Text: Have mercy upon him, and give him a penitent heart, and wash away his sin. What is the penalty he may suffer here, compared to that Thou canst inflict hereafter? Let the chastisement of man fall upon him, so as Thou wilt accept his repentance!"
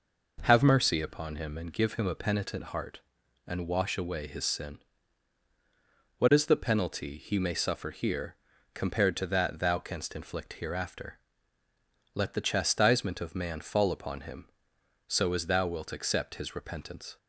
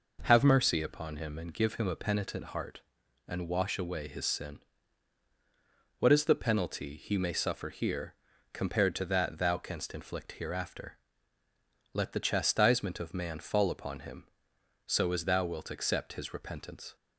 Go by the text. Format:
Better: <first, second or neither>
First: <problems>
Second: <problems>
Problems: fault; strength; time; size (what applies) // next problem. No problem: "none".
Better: neither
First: none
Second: none